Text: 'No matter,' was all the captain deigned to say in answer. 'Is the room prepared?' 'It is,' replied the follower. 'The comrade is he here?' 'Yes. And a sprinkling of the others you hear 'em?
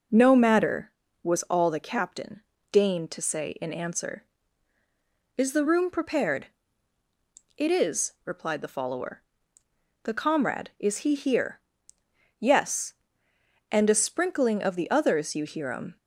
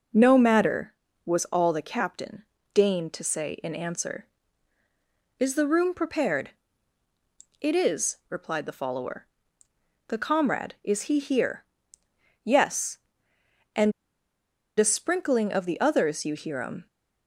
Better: first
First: pauses between "captain" and "deigned"; slight; at 2.4 s; 0.30 s long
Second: pauses between "captain" and "deigned"; slight; at 2.4 s; 0.30 s long // pauses between "And" and "a"; noticeable; at 13.9 s; 0.87 s long

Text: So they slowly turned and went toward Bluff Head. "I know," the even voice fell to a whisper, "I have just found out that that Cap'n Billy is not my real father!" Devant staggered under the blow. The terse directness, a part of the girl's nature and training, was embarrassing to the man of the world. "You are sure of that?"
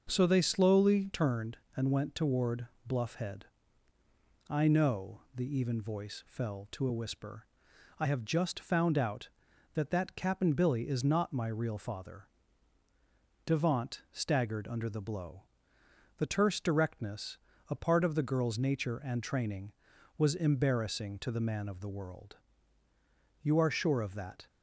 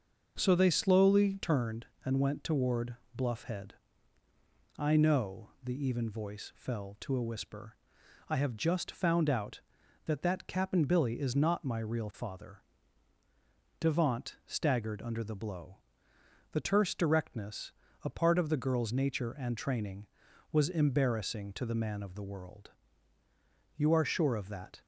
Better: neither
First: pauses between "toward" and "Bluff"; slight; at 2.6 s; 0.18 s long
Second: pauses between "toward" and "Bluff"; slight; at 2.9 s; 0.18 s long

